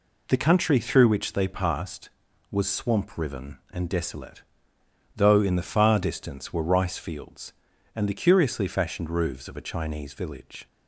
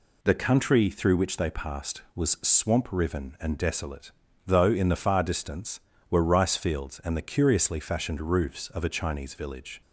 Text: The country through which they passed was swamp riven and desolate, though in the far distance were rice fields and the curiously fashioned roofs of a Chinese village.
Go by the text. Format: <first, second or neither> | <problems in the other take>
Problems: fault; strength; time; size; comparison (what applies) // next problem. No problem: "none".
neither | none